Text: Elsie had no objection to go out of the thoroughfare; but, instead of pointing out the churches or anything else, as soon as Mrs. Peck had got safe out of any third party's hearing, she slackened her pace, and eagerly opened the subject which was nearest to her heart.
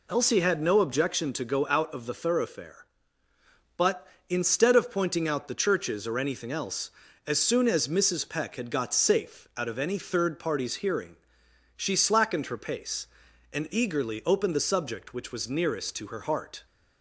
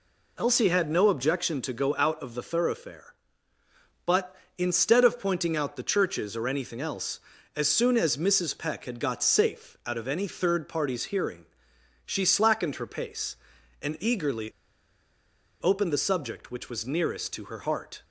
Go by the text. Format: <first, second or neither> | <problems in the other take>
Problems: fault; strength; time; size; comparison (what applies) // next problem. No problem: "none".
first | pauses between "eagerly" and "opened"; at 14.4 s; 1.1 s long